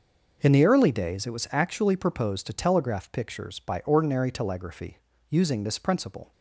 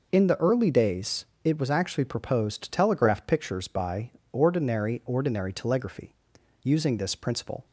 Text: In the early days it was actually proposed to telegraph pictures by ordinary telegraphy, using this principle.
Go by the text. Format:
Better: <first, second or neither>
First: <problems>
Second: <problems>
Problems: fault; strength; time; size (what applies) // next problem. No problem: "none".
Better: first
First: none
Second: pauses between "days" and "it"; slight; at 1.2 s; 0.18 s long // pauses between "by" and "ordinary"; slight; at 4.0 s; 0.22 s long // says "ordinary" twice; at 5.0 s